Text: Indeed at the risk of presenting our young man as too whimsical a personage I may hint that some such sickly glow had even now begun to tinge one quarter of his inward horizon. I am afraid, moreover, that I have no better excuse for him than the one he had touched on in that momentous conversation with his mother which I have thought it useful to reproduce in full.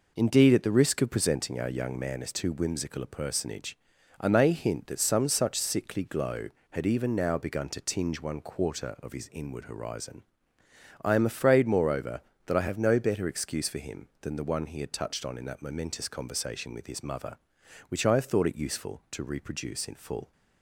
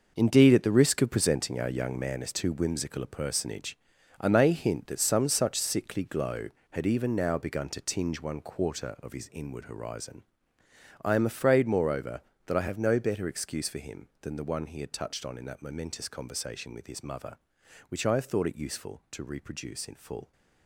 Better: first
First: pauses between "personage" and "I"; at 3.7 s; 0.42 s long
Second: gets quieter; strong; throughout; 11 dB // pauses between "personage" and "I"; at 3.7 s; 0.42 s long

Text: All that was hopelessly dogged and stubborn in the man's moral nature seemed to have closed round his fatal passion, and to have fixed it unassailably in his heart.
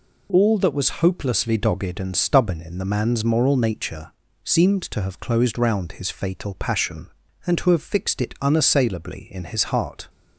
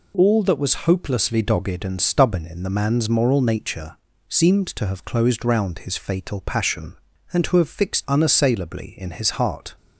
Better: first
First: pauses between "nature" and "seemed"; slight; at 4.1 s; 0.32 s long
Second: pauses between "nature" and "seemed"; slight; at 3.9 s; 0.32 s long // skips "it"; at 8.0 s

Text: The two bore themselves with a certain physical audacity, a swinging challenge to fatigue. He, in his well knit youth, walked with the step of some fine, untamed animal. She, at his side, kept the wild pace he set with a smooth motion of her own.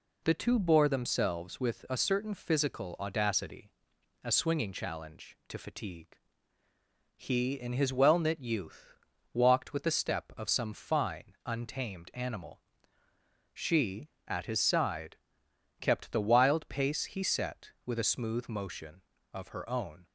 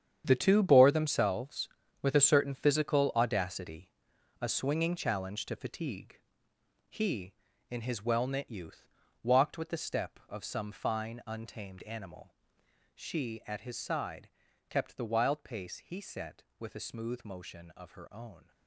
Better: first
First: none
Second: gets quieter; strong; throughout; 12.5 dB

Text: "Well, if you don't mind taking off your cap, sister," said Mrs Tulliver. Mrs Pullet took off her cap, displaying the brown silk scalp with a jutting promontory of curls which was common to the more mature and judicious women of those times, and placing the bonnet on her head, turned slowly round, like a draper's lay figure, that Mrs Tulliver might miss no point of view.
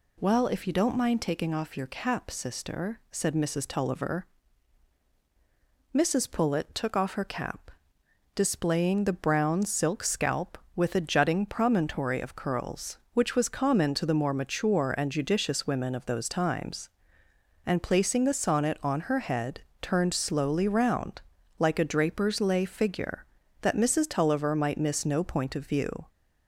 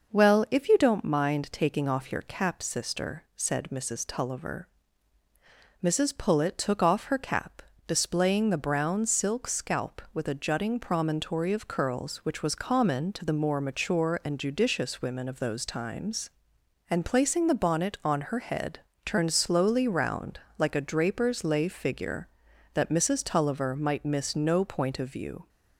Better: second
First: says "sonnet" for "bonnet"; at 18.3 s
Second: none

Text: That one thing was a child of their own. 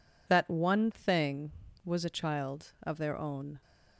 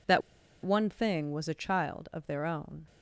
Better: first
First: none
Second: pauses between "That" and "one"; at 0.2 s; 0.42 s long

